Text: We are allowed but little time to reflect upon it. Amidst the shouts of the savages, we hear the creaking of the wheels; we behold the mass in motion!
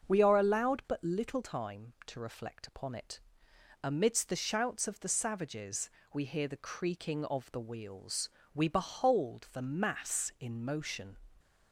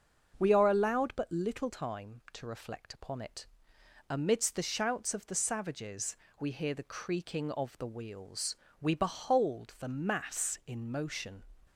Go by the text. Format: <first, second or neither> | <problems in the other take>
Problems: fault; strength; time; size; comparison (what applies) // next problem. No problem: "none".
neither | starts louder than the rest; the same in both